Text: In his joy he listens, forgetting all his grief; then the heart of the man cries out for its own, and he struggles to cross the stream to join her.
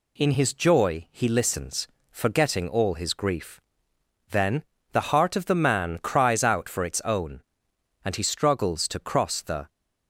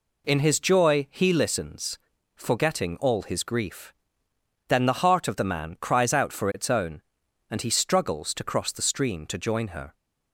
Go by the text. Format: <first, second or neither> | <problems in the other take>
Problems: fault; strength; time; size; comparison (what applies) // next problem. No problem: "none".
second | pauses between "then" and "the"; slight; at 4.6 s; 0.30 s long // stops before "stream to join her"; at 9.6 s